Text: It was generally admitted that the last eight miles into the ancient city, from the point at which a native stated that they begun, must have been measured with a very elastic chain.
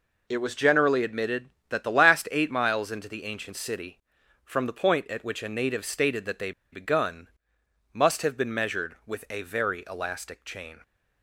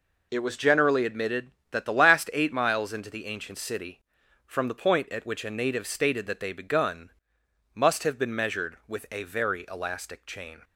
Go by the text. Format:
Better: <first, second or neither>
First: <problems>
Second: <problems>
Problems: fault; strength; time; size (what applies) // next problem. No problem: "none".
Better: second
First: pauses between "they" and "begun"; slight; at 6.5 s; 0.20 s long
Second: none